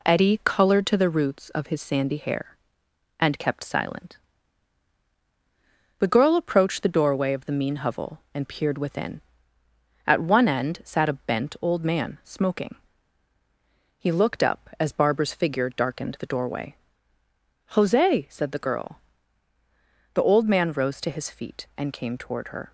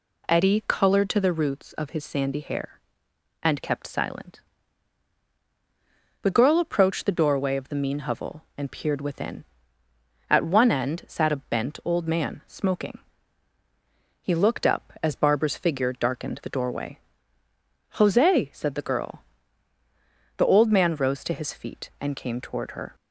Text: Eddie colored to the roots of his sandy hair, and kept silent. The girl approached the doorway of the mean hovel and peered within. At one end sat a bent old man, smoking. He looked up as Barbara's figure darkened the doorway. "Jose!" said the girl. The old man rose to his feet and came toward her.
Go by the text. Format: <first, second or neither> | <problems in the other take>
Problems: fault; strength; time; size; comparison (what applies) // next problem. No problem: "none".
second | gets quieter; throughout; 3.5 dB